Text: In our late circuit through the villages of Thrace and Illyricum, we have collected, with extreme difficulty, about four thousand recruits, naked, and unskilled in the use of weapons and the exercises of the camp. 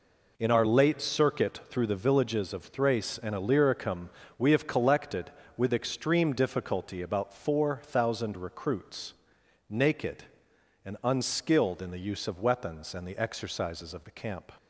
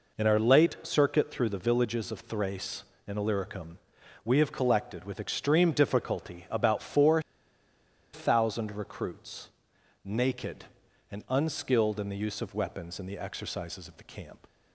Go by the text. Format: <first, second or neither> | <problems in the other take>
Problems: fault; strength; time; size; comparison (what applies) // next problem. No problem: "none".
first | pauses between "four" and "thousand"; noticeable; at 7.1 s; 0.93 s long